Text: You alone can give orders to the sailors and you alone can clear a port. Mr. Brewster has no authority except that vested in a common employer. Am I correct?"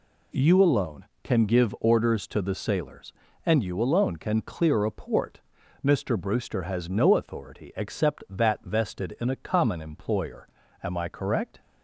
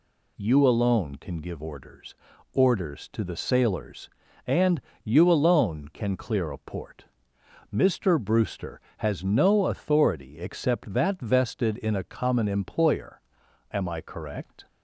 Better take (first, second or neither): first